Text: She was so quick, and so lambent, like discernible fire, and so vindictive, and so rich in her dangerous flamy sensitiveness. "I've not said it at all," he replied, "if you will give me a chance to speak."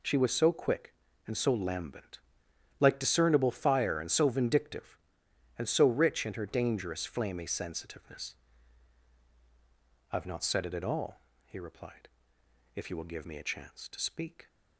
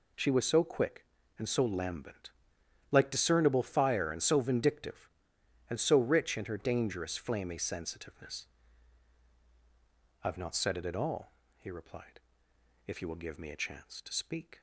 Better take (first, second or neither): neither